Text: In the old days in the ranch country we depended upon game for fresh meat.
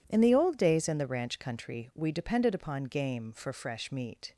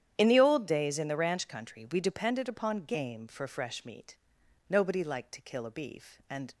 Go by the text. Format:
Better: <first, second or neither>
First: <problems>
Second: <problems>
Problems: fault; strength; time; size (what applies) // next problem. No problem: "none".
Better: first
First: none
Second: starts louder than the rest; strong; until 1.1 s; 10 dB // goes on to say "Nobody liked to kill a beef and"; strong; from 4.6 s on; 1.8 s long